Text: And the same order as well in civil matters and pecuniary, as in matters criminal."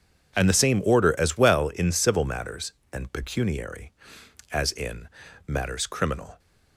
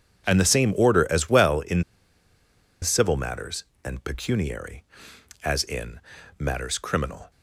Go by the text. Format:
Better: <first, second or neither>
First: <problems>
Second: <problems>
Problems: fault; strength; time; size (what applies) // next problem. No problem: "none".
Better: first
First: pauses between "in" and "matters"; at 5.0 s; 0.38 s long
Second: pauses between "in" and "civil"; at 1.8 s; 0.98 s long // pauses between "in" and "matters"; at 6.0 s; 0.38 s long